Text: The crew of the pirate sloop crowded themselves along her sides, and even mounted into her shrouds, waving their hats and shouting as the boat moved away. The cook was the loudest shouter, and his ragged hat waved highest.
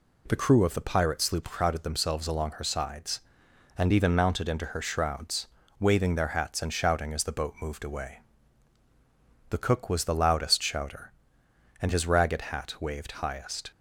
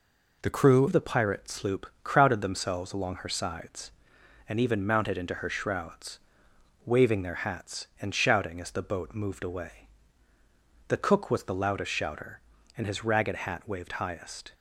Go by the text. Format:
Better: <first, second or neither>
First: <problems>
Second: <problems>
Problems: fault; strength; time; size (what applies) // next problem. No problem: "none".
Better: first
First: none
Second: changes voice at "of"; from 0.8 s on; 13.7 s long // pauses between "sloop" and "crowded"; slight; at 1.8 s; 0.16 s long